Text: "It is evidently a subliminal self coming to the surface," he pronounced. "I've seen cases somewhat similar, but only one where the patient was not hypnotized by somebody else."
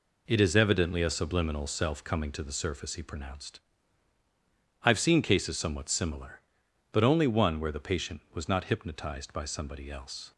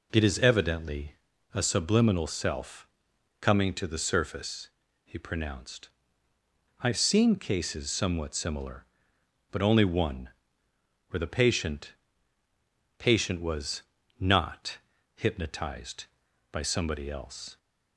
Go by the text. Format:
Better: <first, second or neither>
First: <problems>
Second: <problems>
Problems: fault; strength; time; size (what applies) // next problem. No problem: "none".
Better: first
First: none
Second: pauses between "evidently" and "a"; at 1.1 s; 0.40 s long // pauses between "self" and "coming"; noticeable; at 2.8 s; 0.52 s long // pauses between "one" and "where"; noticeable; at 10.3 s; 0.78 s long // says "patient" twice; at 12.9 s // pauses between "was" and "not"; slight; at 13.8 s; 0.36 s long // pauses between "not" and "hypnotized"; at 14.7 s; 0.38 s long